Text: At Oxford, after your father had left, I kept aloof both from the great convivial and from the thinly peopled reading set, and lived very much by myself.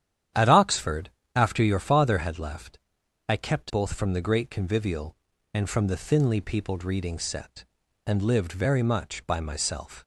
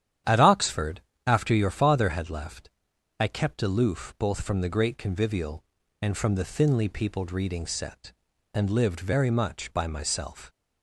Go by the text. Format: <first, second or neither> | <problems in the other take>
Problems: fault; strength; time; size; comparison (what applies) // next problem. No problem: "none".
second | starts louder than the rest; strong; until 1.6 s; 10 dB; strong in the second // skips "aloof"; at 3.6 s